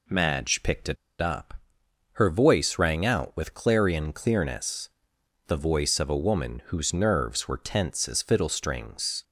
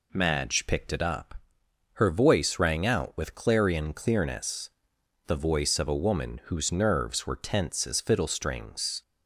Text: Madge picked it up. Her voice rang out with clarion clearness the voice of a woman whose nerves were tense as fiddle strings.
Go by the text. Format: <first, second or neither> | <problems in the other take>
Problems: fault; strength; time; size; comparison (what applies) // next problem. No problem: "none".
second | pauses between "it" and "up"; slight; at 0.9 s; 0.25 s long // pauses between "clearness" and "the"; noticeable; at 4.8 s; 0.58 s long; noticeable in the second